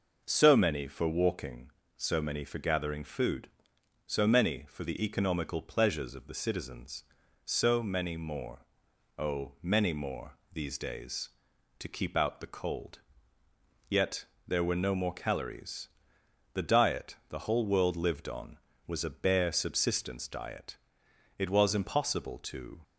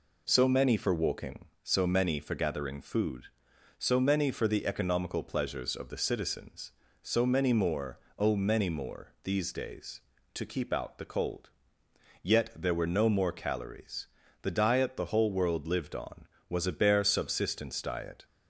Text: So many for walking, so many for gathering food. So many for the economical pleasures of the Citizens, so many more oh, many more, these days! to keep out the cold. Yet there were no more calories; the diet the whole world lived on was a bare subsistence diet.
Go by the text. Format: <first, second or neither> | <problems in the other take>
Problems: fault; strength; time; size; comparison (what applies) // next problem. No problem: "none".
second | pauses between "more" and "oh"; noticeable; at 8.6 s; 0.54 s long; slight in the second // pauses between "Yet" and "there"; slight; at 14.2 s; 0.24 s long // goes on to say "It was impossible to"; from 21.3 s on; 1.4 s long